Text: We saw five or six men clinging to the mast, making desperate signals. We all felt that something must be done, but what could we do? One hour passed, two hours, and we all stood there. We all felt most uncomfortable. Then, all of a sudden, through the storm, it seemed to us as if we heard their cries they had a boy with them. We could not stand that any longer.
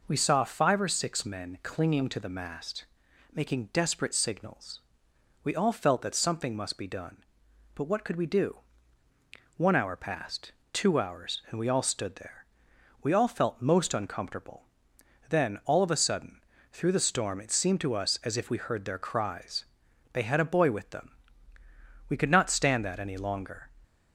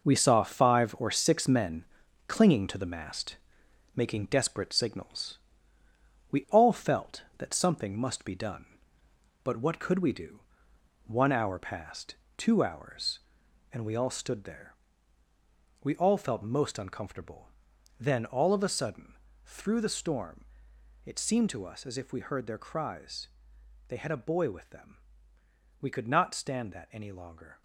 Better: first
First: pauses between "cries" and "they"; noticeable; at 19.6 s; 0.46 s long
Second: gets quieter; strong; throughout; 9 dB // pauses between "men" and "clinging"; at 1.8 s; 0.42 s long // pauses between "cries" and "they"; noticeable; at 23.2 s; 0.60 s long

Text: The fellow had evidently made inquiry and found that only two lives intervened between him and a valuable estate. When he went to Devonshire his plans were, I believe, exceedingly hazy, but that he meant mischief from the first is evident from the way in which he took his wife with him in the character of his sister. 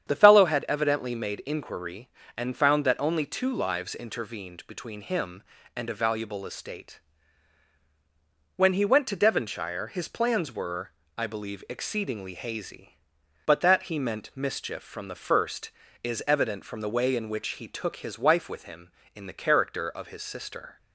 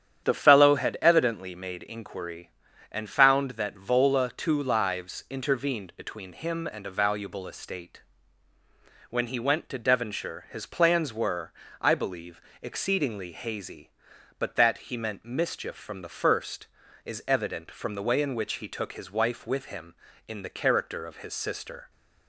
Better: first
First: starts louder than the rest; strong; until 1.1 s; 8.5 dB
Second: starts louder than the rest; strong; until 1.2 s; 9.5 dB // says "vola" for "only"; at 3.7 s

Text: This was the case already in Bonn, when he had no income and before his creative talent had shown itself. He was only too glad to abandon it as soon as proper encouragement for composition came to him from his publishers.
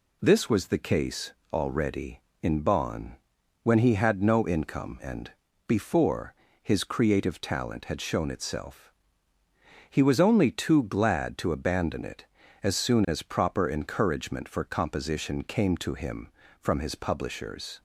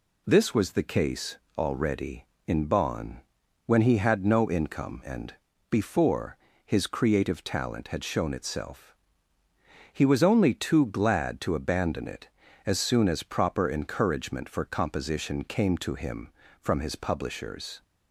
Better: neither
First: pauses between "case" and "already"; slight; at 1.3 s; 0.22 s long // pauses between "and" and "before"; slight; at 5.3 s; 0.34 s long // pauses between "before" and "his"; slight; at 6.3 s; 0.28 s long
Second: pauses between "case" and "already"; slight; at 1.3 s; 0.22 s long // pauses between "and" and "before"; slight; at 5.3 s; 0.34 s long // pauses between "before" and "his"; slight; at 6.3 s; 0.28 s long

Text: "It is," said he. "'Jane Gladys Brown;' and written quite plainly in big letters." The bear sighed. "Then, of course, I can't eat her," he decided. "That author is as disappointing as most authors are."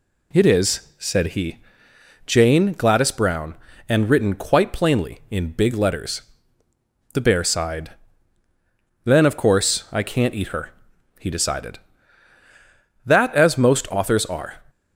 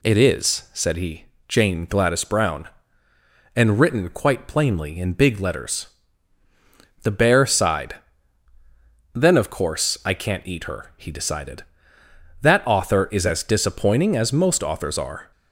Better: second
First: skips "author is as disappointing"; at 13.3 s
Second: none

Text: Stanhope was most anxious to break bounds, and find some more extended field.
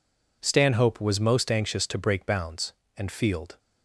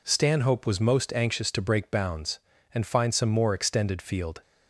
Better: second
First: skips "find some more extended"; at 3.1 s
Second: none

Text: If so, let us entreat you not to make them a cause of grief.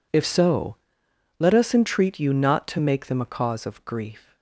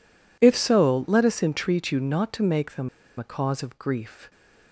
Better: first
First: none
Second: pauses between "them" and "a"; slight; at 2.8 s; 0.31 s long

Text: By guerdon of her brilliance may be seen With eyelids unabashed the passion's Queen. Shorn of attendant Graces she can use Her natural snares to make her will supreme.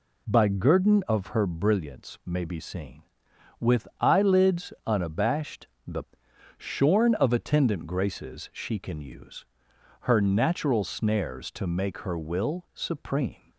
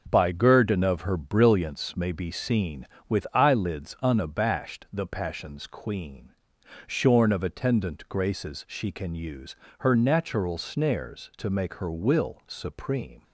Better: second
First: pauses between "unabashed" and "the"; slight; at 5.6 s; 0.18 s long // skips "passion's Queen"; at 6.2 s // pauses between "use" and "Her"; noticeable; at 9.4 s; 0.58 s long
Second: pauses between "use" and "Her"; slight; at 9.5 s; 0.24 s long

